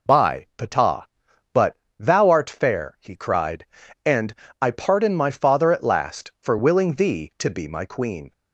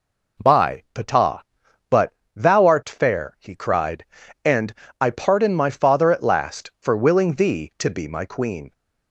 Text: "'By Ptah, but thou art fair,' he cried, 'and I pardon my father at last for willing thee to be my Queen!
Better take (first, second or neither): second